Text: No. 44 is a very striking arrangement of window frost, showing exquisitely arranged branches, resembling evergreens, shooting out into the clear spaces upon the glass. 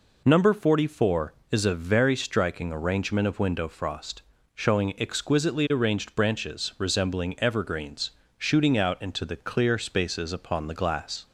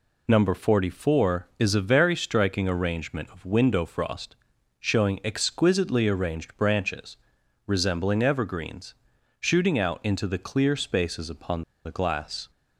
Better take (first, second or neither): first